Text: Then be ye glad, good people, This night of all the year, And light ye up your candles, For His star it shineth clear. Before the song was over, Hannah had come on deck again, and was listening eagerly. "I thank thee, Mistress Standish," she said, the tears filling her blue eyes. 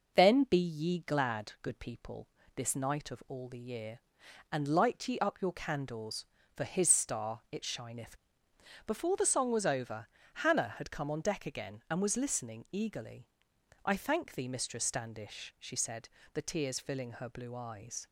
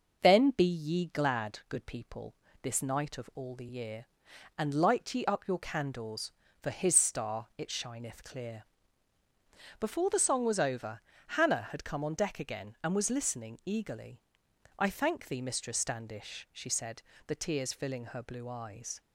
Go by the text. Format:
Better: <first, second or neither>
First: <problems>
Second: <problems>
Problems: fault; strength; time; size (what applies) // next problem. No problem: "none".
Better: second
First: skips "clear"; at 8.5 s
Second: none